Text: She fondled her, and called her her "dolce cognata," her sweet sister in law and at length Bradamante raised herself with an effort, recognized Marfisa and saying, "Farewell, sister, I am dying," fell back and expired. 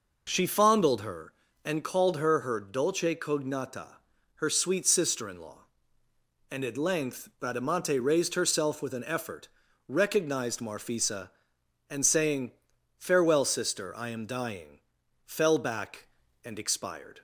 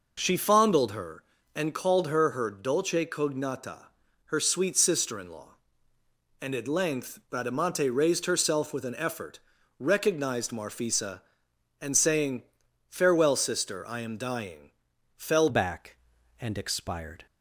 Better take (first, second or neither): first